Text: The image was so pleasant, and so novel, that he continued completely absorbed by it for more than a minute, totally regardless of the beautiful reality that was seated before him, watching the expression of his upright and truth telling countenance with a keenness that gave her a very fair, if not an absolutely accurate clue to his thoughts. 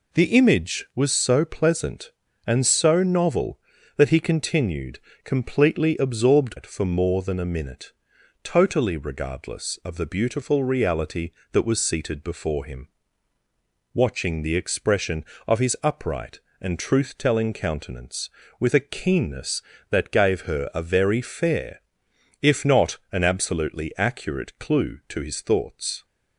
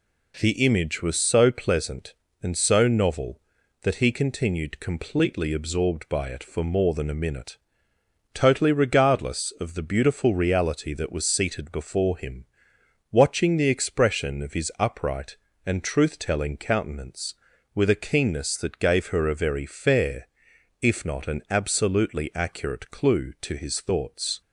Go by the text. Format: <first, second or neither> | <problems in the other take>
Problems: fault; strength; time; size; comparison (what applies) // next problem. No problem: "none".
second | pauses between "continued" and "completely"; slight; at 4.9 s; 0.24 s long // skips "by"; at 6.5 s